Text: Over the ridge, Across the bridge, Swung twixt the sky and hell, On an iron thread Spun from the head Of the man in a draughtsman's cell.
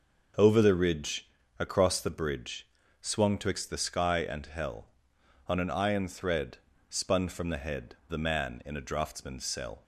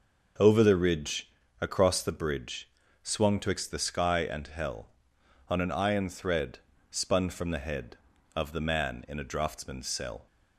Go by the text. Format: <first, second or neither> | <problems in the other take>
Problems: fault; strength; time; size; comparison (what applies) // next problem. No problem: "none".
second | pauses between "thread" and "Spun"; slight; at 6.5 s; 0.32 s long; slight in the second // skips "Of"; at 8.0 s